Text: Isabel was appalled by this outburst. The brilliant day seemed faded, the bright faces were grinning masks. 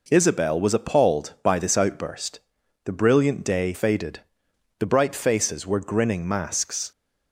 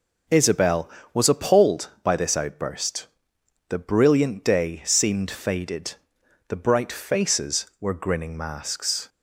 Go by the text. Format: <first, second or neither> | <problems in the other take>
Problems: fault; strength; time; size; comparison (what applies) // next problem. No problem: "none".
second | skips "seemed"; at 3.7 s